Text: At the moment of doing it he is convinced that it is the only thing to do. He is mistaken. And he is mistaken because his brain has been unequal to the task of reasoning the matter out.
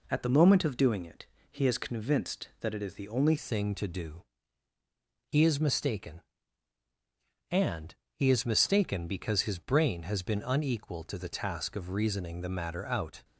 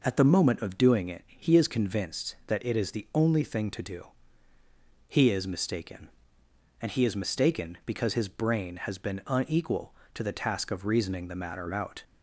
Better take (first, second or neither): second